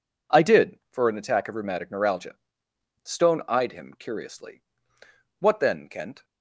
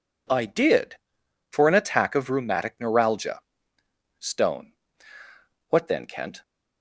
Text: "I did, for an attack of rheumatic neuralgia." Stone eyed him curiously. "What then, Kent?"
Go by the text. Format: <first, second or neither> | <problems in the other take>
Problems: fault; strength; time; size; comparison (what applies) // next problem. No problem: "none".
first | skips "eyed him curiously"; at 5.2 s